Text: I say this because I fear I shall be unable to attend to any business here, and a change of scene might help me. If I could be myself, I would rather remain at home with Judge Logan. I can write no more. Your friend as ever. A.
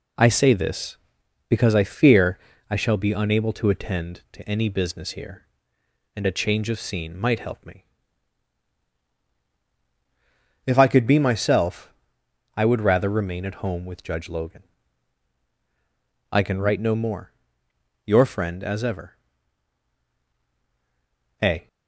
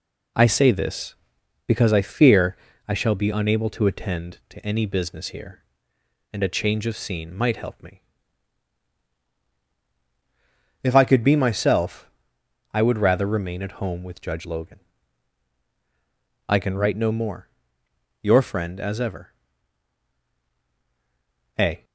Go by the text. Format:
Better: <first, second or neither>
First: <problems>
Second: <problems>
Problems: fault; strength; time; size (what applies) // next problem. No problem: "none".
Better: neither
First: pauses between "fear" and "I"; slight; at 2.3 s; 0.32 s long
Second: pauses between "fear" and "I"; slight; at 2.5 s; 0.32 s long